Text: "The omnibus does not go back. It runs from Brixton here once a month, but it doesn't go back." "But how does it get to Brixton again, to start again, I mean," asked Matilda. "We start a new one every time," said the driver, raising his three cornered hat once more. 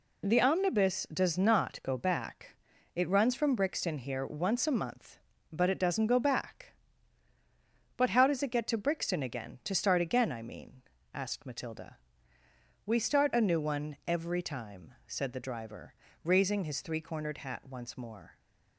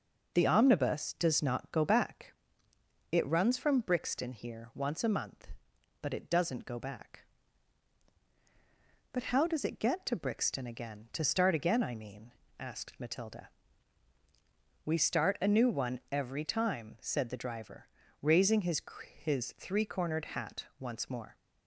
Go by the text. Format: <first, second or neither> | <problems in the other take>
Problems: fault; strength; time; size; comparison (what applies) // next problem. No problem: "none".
first | says "his" twice; at 19.2 s